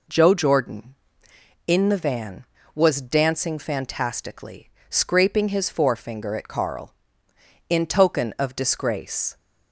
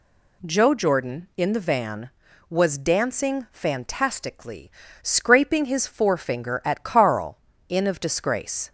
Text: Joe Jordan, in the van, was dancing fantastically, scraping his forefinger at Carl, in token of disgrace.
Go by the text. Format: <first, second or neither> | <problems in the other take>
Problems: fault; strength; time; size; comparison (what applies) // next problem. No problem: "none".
first | skips "token"; at 7.8 s